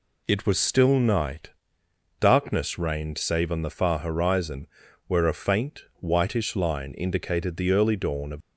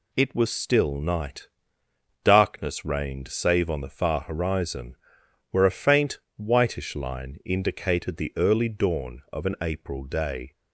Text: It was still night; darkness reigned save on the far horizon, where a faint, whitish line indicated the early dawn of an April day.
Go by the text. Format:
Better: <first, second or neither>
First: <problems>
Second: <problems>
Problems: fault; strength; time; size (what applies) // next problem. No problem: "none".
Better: second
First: stops before "an April day"; at 8.4 s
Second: none